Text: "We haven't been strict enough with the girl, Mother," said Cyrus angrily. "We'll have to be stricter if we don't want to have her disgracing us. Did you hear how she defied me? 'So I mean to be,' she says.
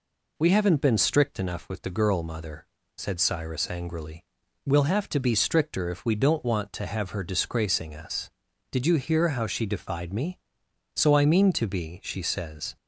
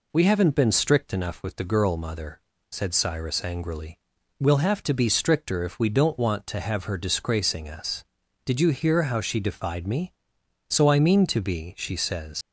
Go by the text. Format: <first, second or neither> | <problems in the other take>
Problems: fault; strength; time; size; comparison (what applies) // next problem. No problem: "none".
first | leaves "says" unfinished; at 12.4 s; 90 ms